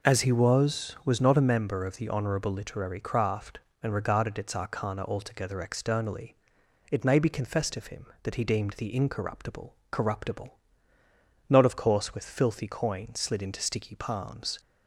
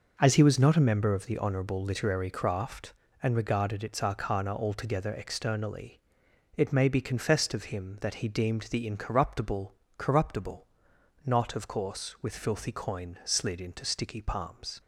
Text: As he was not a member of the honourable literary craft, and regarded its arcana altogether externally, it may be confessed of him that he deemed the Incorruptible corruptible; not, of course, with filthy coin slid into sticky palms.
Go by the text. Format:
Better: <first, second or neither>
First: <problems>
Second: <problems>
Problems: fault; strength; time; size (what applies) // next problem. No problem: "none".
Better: second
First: says "was" twice; at 1.0 s // pauses between "Incorruptible" and "corruptible"; slight; at 9.7 s; 0.16 s long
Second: pauses between "Incorruptible" and "corruptible"; slight; at 9.7 s; 0.24 s long